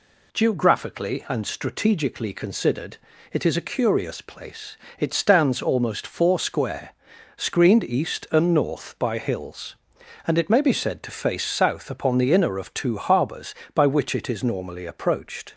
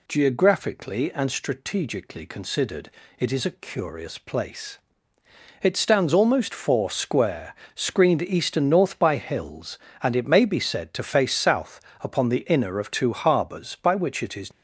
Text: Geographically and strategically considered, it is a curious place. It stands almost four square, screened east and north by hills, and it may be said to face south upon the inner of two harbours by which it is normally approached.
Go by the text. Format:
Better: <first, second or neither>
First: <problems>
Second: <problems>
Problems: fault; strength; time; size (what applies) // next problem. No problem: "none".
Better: first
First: none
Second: pauses between "south" and "upon"; slight; at 11.7 s; 0.22 s long // stops before "normally approached"; at 14.5 s